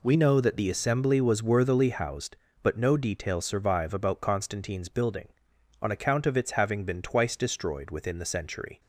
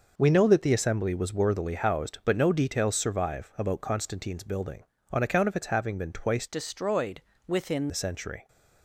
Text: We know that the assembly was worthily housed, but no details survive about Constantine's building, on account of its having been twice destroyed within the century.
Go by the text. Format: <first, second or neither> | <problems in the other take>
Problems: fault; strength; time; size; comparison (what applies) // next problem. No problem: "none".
first | changes voice from "destroyed" to "within"; from 6.4 to 7.8 s; 1.4 s long // pauses between "destroyed" and "within"; slight; at 7.2 s; 0.24 s long